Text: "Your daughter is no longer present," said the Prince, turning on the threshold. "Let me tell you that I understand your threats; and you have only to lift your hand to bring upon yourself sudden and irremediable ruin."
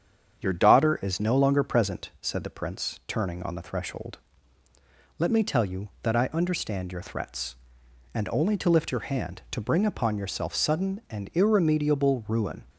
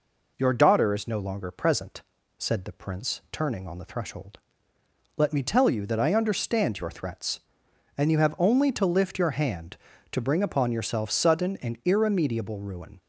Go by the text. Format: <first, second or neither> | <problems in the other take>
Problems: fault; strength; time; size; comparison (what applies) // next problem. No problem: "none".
second | starts louder than the rest; strong; until 1.4 s; 8 dB // skips "you have"; at 8.2 s